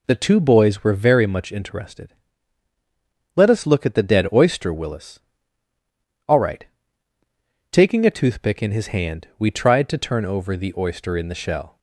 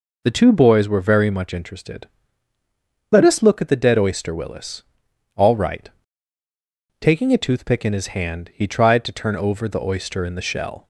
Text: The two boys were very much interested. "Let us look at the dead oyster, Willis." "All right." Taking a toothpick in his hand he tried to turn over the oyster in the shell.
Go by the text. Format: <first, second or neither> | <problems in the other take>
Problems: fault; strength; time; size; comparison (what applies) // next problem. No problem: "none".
second | says "we" for "he"; at 9.3 s